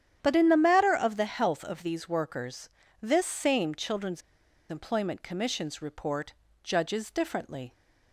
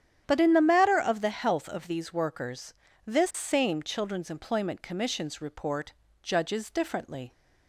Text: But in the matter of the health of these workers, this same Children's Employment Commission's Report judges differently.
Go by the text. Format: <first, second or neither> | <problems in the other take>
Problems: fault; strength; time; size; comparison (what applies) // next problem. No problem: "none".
second | starts louder than the rest; strong; until 1.2 s; 9.5 dB; strong in the second // pauses between "Children's" and "Employment"; noticeable; at 4.2 s; 0.49 s long // pauses between "Report" and "judges"; slight; at 6.3 s; 0.32 s long; slight in the second